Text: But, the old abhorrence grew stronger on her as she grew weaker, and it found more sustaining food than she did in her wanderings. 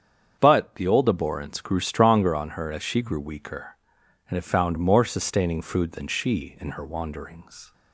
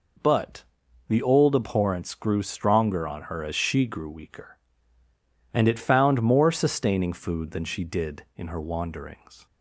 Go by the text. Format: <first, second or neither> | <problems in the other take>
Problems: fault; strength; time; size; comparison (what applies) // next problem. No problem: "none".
second | starts louder than the rest; strong; until 1.4 s; 7.5 dB // skips "did"; at 6.5 s